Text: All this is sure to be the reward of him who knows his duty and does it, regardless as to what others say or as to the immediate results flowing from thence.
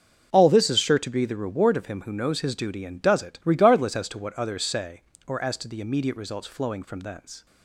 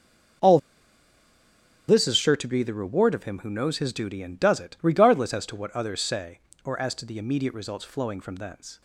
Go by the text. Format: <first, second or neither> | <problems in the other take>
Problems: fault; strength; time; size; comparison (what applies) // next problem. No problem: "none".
first | starts louder than the rest; until 2.7 s; 6.5 dB; also in the first // pauses between "All" and "this"; strong; at 0.5 s; 1.2 s long